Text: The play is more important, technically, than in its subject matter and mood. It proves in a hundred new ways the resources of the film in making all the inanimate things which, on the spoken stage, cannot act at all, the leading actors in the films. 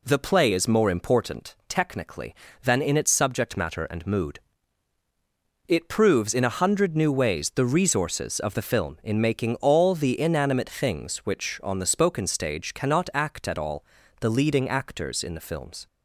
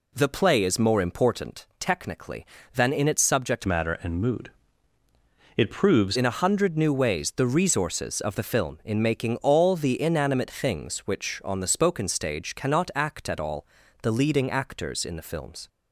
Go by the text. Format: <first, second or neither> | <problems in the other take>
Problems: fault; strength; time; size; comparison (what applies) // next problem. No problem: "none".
first | changes voice from "matter" to "proves"; from 3.6 to 6.1 s; 2.5 s long